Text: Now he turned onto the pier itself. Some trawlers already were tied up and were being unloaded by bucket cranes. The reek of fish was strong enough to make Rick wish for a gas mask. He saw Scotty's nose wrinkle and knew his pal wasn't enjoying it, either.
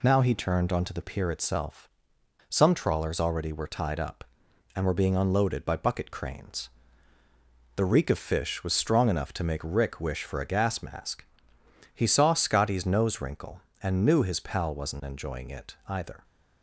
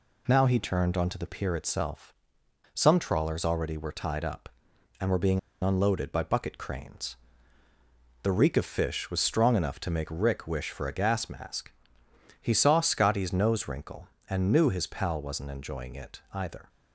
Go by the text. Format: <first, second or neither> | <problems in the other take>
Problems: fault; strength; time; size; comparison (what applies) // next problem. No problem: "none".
first | pauses between "being" and "unloaded"; slight; at 5.3 s; 0.22 s long